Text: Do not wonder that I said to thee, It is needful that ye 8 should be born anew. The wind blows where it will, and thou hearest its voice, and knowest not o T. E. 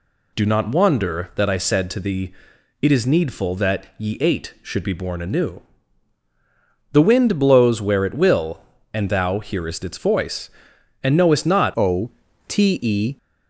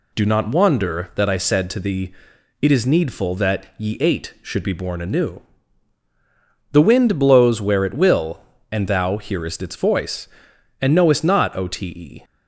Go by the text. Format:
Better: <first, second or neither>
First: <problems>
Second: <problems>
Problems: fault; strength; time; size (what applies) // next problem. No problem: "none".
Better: second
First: changes voice at "o"; from 11.7 s on; 1.4 s long // pauses between "o" and "T"; slight; at 12.1 s; 0.36 s long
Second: none